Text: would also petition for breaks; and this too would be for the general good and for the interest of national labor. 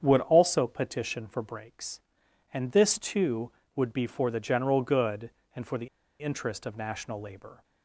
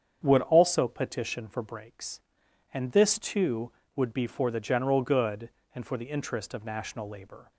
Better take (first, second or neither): second